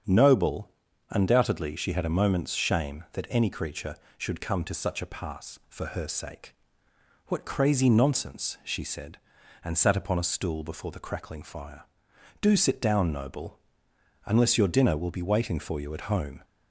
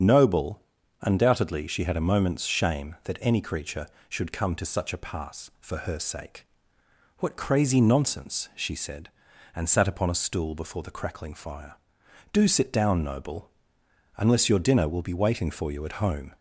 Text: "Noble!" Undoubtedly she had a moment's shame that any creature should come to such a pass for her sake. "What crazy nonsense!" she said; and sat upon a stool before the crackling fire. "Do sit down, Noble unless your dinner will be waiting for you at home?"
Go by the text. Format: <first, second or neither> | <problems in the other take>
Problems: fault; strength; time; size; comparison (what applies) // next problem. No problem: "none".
first | loses the start of "Noble"; at 0.0 s; 35 ms // starts louder than the rest; strong; until 1.4 s; 7.5 dB; strong in the first // pauses between "Noble" and "unless"; noticeable; at 13.5 s; 0.66 s long; noticeable in the first